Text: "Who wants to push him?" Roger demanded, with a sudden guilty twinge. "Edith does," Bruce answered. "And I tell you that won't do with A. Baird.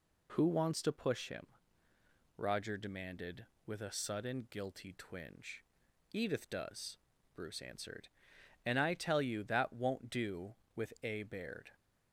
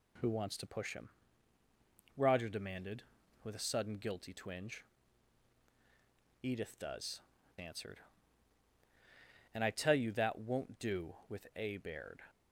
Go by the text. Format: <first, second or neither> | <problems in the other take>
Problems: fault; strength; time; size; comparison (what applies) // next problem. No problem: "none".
first | skips "Bruce"; at 7.3 s